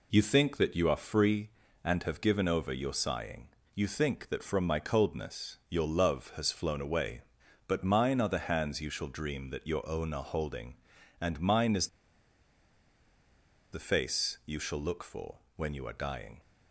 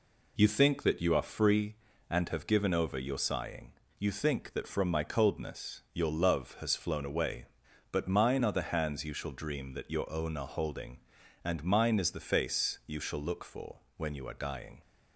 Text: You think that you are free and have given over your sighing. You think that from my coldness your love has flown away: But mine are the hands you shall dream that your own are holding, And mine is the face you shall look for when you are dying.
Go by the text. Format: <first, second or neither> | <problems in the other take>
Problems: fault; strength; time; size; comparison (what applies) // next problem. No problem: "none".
second | pauses between "is" and "the"; strong; at 11.8 s; 1.8 s long // pauses between "for" and "when"; slight; at 15.3 s; 0.18 s long; slight in the second